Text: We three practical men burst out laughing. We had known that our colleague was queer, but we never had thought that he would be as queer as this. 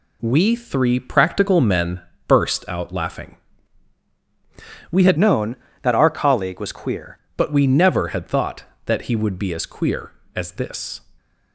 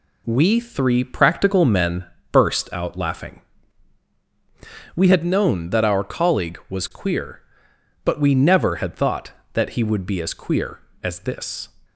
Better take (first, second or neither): second